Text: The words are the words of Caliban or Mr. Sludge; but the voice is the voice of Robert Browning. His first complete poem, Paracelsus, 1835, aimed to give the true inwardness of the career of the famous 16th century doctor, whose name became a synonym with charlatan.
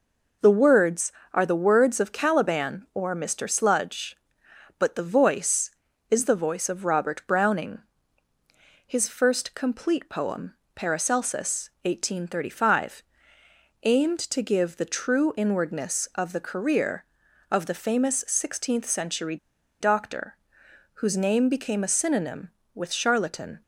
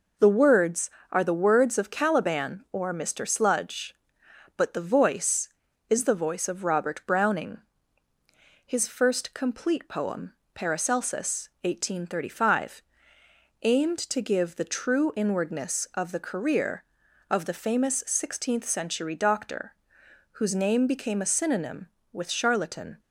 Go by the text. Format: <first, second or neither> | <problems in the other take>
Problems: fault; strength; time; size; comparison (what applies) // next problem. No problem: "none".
second | pauses between "century" and "doctor"; at 19.3 s; 0.43 s long